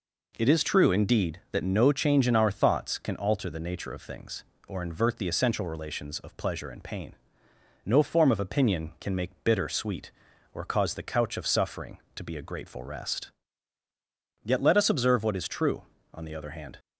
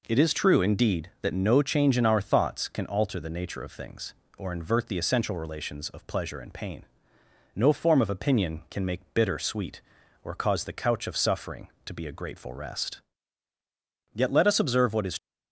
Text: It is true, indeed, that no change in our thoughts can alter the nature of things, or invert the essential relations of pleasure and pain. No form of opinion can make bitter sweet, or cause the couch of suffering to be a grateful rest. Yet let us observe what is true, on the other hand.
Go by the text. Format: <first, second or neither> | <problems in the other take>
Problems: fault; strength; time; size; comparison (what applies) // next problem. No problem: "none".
first | stops before "true on the other hand"; at 15.1 s